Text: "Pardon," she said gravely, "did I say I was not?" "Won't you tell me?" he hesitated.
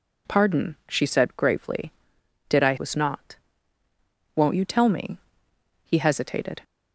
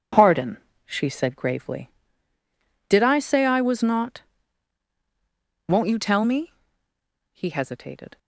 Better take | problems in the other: second | skips "say I"; at 2.7 s

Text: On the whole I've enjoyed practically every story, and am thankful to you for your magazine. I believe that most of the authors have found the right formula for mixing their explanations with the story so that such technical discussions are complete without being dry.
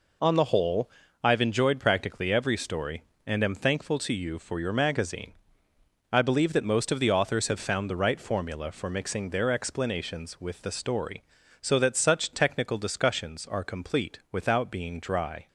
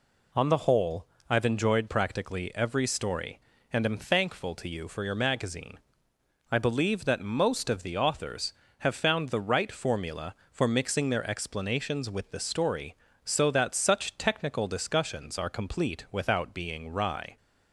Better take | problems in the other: first | pauses between "whole" and "I've"; slight; at 1.0 s; 0.24 s long; slight in the first // says "wry" for "dry"; at 16.9 s

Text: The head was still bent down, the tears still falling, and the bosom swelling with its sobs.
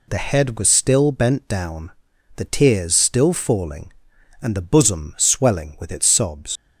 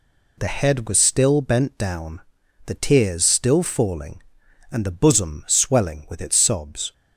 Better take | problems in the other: second | leaves "sobs" unfinished; at 6.5 s; 75 ms

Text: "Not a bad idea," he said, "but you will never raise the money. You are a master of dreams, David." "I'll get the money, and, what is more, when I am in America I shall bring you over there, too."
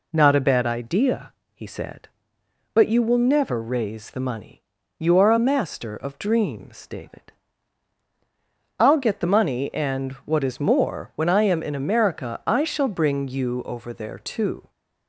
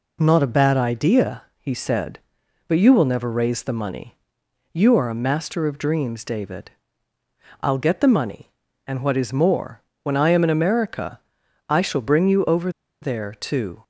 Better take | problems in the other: first | pauses between "America" and "I"; noticeable; at 11.2 s; 0.48 s long // pauses between "over" and "there"; slight; at 12.6 s; 0.32 s long

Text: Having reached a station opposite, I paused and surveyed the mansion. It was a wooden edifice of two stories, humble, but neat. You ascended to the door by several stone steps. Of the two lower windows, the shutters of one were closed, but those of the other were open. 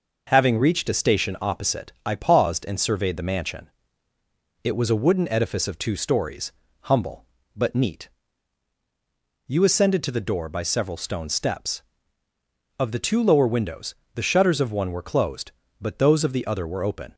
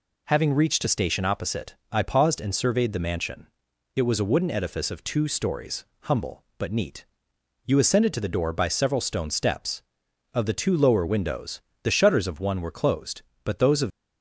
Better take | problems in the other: first | stops before "the other were open"; at 13.8 s

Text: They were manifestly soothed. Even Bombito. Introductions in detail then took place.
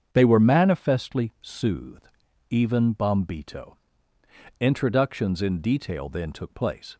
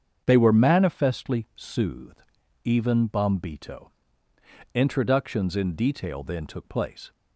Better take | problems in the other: neither | starts louder than the rest; strong; the same in both

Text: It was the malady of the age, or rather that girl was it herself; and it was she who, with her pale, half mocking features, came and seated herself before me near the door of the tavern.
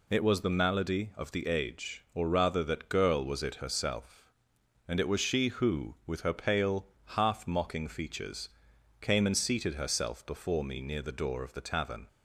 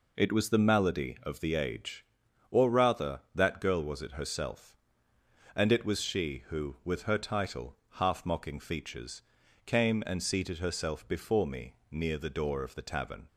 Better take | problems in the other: first | says "title" for "pale"; at 7.1 s // pauses between "me" and "near"; slight; at 11.7 s; 0.16 s long

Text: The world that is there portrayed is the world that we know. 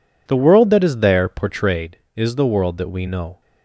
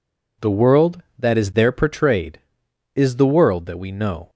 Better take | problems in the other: neither | none

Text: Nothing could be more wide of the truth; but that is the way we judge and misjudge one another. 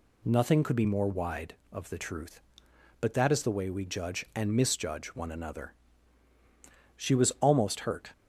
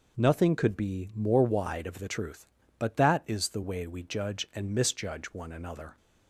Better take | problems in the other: second | goes on to say "She was almost hurt"; noticeable; from 6.9 s on; 1.1 s long

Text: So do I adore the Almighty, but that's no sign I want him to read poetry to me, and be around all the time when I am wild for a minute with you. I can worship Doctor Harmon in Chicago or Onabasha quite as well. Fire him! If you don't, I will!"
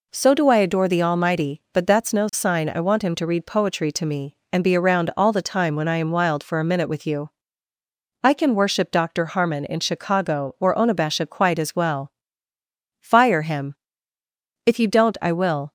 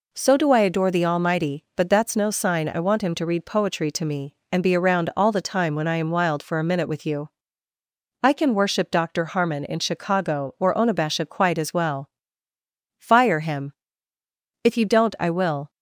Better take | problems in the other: neither | none

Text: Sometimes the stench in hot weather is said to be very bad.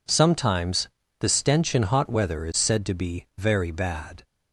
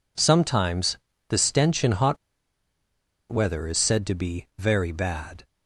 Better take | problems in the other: first | pauses between "Sometimes" and "the"; slight; at 0.9 s; 0.30 s long; slight in the first // pauses between "hot" and "weather"; at 2.1 s; 1.1 s long

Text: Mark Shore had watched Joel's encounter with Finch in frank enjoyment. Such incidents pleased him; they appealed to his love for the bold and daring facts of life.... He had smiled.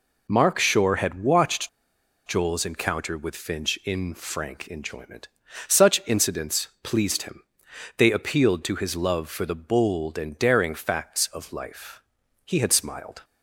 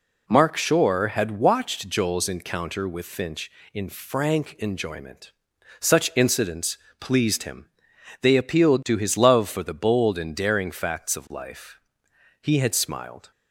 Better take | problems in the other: second | pauses between "watched" and "Joel's"; noticeable; at 1.6 s; 0.56 s long // pauses between "incidents" and "pleased"; slight; at 6.6 s; 0.16 s long; slight in the second

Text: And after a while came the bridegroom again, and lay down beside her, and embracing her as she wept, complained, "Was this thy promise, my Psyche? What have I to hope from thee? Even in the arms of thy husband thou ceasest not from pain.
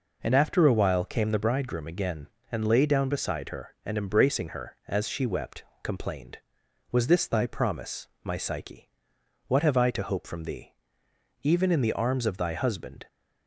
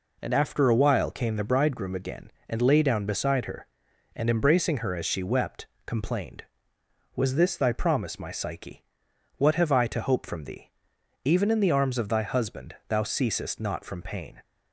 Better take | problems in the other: second | stops before "thou ceasest not from pain"; at 13.0 s

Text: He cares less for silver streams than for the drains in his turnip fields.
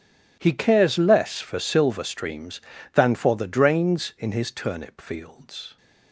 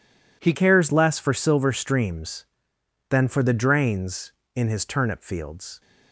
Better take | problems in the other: first | changes voice at "cares"; from 0.5 s on; 5.3 s long

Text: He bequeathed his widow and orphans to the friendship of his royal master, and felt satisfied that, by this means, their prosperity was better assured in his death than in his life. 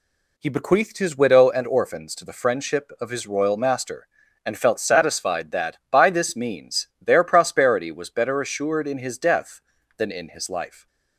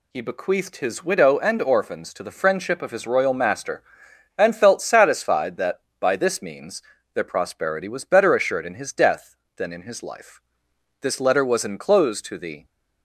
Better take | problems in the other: first | goes on to say "This letter was enclosed to the"; from 11.0 s on; 1.6 s long

